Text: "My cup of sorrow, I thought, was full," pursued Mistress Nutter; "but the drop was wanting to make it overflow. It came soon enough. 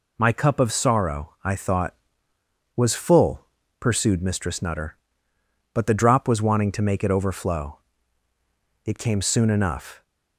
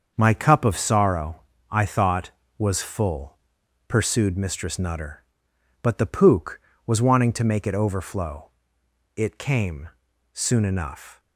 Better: first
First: none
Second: starts louder than the rest; until 1.1 s; 6.5 dB // says "pook" for "drop"; at 6.0 s // pauses between "came" and "soon"; at 9.8 s; 0.42 s long

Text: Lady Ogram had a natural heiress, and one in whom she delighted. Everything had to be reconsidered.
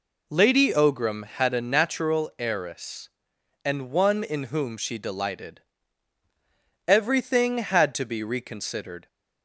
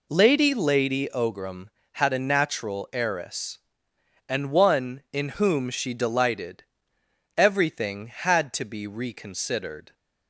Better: first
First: none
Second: says "Lady" twice; at 0.5 s

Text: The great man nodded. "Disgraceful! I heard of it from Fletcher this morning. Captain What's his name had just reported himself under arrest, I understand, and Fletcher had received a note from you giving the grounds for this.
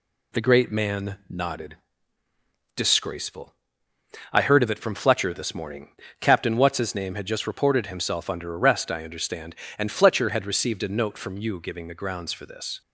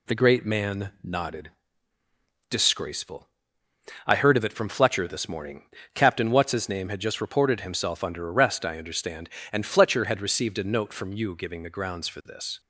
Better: neither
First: none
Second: none

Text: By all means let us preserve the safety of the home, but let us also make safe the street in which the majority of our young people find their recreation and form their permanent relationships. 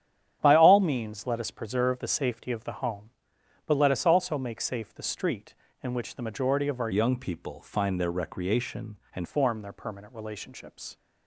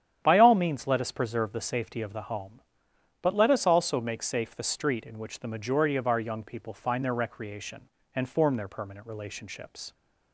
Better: second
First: starts louder than the rest; strong; until 1.4 s; 9.5 dB // changes voice from "young" to "and"; from 6.9 to 9.2 s; 2.3 s long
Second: starts louder than the rest; strong; until 1.2 s; 9.5 dB

